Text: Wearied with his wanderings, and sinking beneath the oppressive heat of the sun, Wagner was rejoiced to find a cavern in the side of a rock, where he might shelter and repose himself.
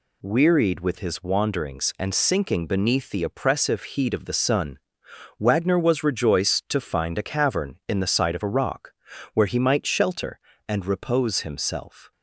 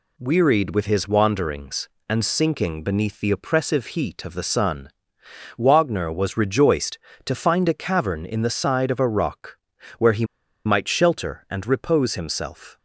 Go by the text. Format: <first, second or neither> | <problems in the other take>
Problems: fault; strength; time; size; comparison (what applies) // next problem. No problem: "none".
first | pauses between "he" and "might"; at 10.2 s; 0.41 s long